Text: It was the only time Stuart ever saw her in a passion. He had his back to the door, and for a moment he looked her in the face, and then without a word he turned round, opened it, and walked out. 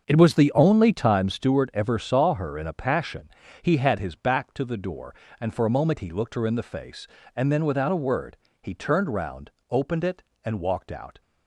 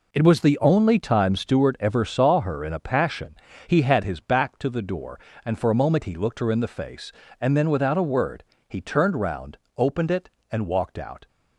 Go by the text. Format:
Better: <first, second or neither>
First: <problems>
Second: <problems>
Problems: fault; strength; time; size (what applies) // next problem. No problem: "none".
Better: second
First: starts louder than the rest; until 1.2 s; 7 dB // pauses between "word" and "he"; slight; at 8.3 s; 0.24 s long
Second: pauses between "word" and "he"; slight; at 8.4 s; 0.24 s long